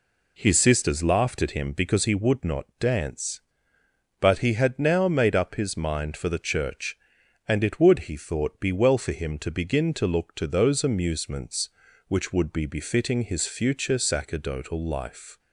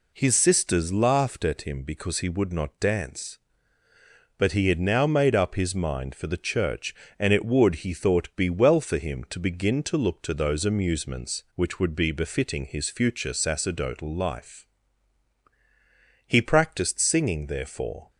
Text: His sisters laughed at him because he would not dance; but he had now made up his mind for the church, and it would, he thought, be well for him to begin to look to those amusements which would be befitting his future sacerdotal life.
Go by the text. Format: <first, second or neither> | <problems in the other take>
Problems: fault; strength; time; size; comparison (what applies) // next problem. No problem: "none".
first | goes on to say "He practised singing therefore"; strong; from 16.2 s on; 1.8 s long